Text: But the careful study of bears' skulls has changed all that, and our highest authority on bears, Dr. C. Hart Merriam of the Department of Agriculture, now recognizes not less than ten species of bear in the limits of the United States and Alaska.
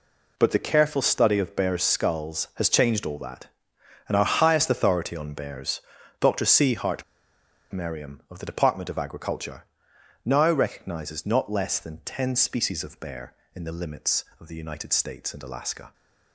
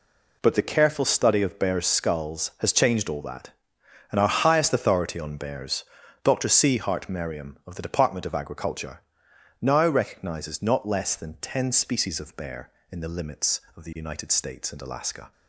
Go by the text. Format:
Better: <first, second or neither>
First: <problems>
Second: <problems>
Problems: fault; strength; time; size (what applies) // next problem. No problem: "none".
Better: second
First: pauses between "Hart" and "Merriam"; noticeable; at 7.0 s; 0.69 s long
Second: none